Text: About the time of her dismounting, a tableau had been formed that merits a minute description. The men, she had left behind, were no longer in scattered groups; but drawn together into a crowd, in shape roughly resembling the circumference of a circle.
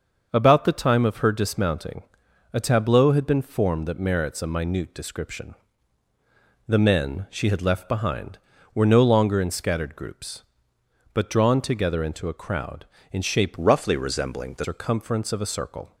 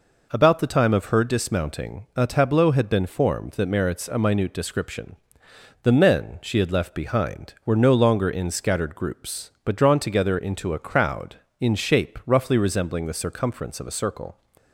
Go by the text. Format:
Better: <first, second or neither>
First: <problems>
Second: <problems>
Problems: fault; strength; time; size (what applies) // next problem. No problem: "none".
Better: second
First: starts louder than the rest; until 1.3 s; 6.5 dB // changes voice from "roughly" to "the"; from 13.5 to 14.6 s; 1.1 s long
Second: none